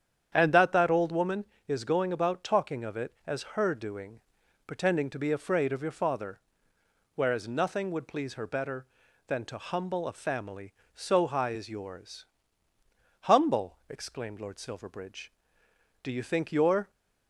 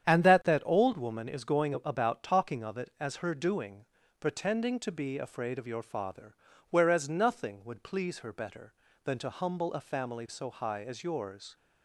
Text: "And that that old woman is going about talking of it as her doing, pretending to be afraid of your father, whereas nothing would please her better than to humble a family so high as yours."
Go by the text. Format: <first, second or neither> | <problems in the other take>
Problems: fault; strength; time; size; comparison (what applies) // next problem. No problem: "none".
second | starts louder than the rest; strong; until 1.3 s; 8.5 dB; strong in the second // goes on to say "Humble exclaimed Lord Silverbridge Do you think your"; strong; from 13.2 s on; 3.6 s long